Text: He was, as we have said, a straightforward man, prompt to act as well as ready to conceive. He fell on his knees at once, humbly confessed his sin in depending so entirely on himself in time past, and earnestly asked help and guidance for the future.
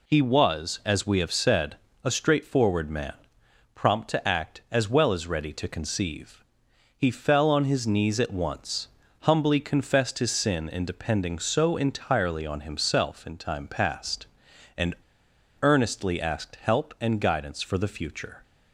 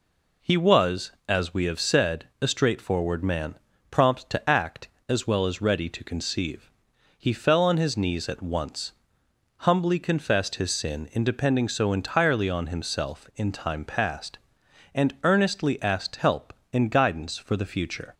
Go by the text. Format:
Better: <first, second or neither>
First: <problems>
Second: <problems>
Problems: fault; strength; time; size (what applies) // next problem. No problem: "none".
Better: second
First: pauses between "and" and "earnestly"; noticeable; at 14.9 s; 0.68 s long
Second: none